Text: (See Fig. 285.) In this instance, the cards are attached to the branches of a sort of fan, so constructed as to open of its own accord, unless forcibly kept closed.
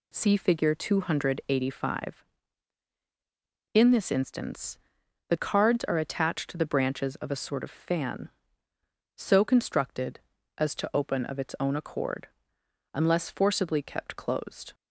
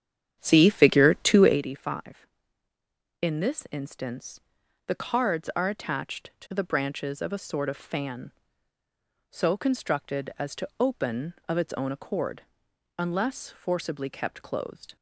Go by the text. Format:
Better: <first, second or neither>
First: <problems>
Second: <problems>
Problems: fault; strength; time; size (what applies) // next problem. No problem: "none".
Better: first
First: none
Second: starts louder than the rest; strong; until 1.6 s; 9 dB